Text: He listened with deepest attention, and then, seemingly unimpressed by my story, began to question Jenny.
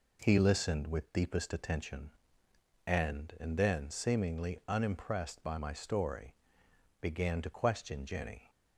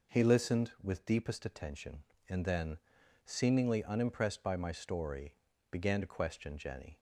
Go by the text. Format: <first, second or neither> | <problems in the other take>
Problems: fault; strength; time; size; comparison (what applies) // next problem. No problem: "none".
second | says "and" twice; at 3.3 s